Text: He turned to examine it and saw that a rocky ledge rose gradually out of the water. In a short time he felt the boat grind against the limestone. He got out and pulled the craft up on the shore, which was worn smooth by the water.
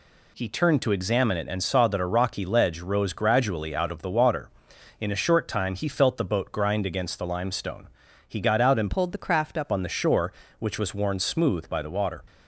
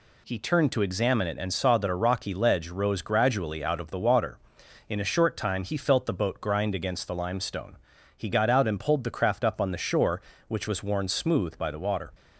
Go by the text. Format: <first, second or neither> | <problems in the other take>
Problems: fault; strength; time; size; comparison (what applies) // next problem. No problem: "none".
second | changes voice from "pulled" to "up"; from 8.9 to 9.7 s; 0.8 s long